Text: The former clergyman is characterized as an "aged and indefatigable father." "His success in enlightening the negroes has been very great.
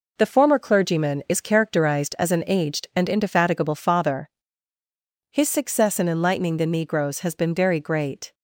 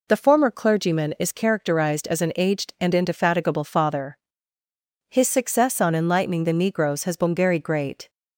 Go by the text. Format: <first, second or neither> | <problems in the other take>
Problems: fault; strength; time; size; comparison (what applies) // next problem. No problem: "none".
first | says "on" for "in"; at 5.7 s